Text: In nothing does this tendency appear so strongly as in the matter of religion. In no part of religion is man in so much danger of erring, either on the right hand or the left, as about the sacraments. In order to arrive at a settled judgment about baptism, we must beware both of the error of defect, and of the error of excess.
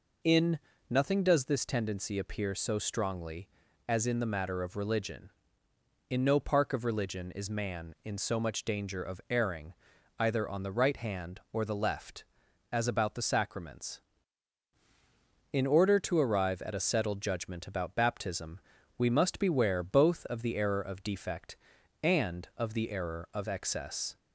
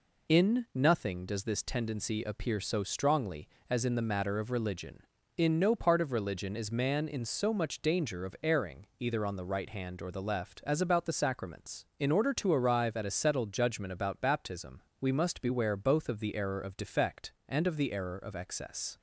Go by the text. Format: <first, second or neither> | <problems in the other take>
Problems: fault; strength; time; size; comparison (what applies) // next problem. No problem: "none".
second | pauses between "In" and "nothing"; slight; at 0.5 s; 0.32 s long // says "park" for "part"; at 6.3 s